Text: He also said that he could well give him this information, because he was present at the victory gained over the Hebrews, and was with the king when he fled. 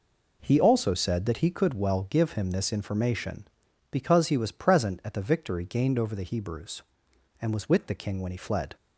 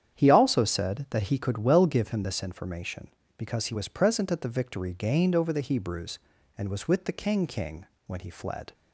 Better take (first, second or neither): first